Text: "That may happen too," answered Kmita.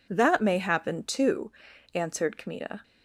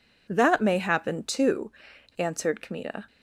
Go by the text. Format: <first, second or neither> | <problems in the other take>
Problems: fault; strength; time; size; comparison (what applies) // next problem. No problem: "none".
neither | none